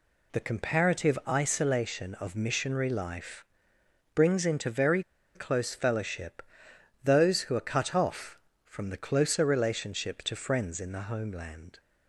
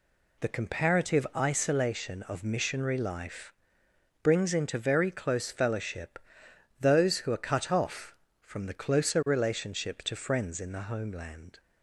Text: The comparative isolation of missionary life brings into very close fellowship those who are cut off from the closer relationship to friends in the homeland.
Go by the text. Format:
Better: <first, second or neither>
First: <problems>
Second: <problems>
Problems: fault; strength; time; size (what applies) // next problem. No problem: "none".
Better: second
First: pauses between "life" and "brings"; noticeable; at 3.4 s; 0.68 s long // pauses between "very" and "close"; slight; at 5.0 s; 0.33 s long // pauses between "fellowship" and "those"; noticeable; at 6.4 s; 0.60 s long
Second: pauses between "life" and "brings"; noticeable; at 3.5 s; 0.68 s long // pauses between "fellowship" and "those"; noticeable; at 6.1 s; 0.60 s long